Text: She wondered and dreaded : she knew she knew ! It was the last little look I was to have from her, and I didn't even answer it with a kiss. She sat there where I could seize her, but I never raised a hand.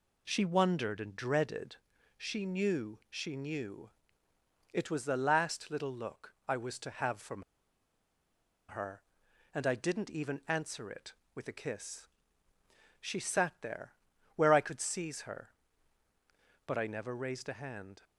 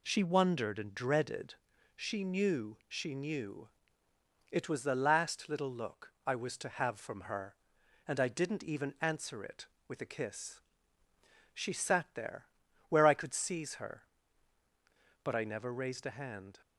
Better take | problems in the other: second | pauses between "from" and "her"; strong; at 7.4 s; 1.2 s long // pauses between "there" and "where"; noticeable; at 13.9 s; 0.46 s long; noticeable in the second

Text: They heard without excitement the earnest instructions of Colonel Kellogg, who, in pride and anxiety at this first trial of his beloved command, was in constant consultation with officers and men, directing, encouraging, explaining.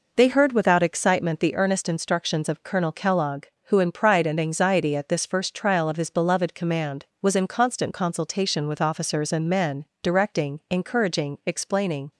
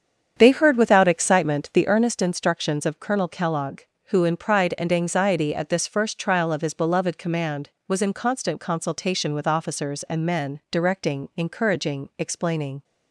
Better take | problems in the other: first | starts louder than the rest; strong; until 2.0 s; 8 dB

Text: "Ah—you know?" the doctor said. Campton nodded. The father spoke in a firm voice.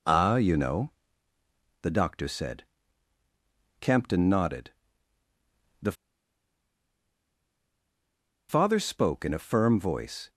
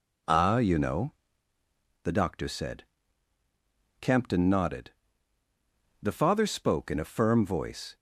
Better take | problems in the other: second | pauses between "The" and "father"; strong; at 5.9 s; 2.5 s long

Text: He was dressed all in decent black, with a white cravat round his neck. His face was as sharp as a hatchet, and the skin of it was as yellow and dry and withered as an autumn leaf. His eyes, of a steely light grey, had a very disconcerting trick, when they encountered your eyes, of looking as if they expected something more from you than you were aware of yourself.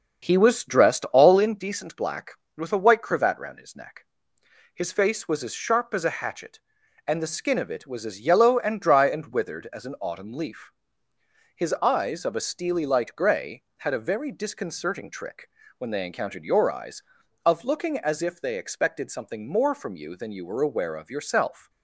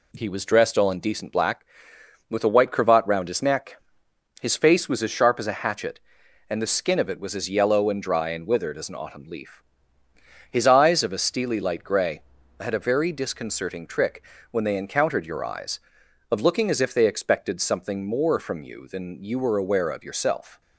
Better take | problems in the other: second | starts louder than the rest; until 1.6 s; 7 dB

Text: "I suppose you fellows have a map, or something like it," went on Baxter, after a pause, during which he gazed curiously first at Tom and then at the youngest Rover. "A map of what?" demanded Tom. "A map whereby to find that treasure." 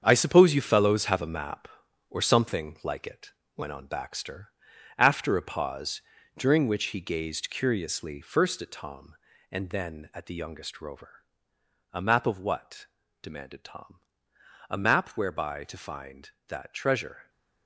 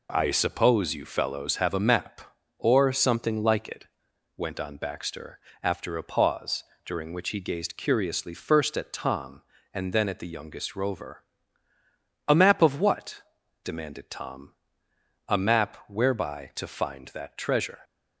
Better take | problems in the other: second | gets quieter; strong; throughout; 10 dB

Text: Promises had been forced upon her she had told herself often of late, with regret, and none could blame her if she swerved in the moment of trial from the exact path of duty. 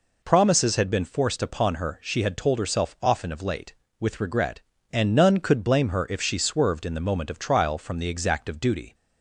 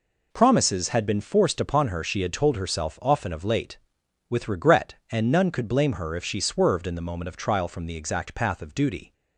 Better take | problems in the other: second | skips "path"; at 8.4 s

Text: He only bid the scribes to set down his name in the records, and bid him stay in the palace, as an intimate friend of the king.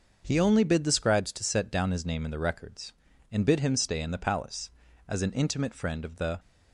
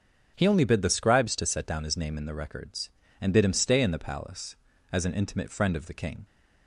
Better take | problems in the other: second | starts louder than the rest; until 1.2 s; 6 dB; strong in the second // stops before "king"; at 6.3 s

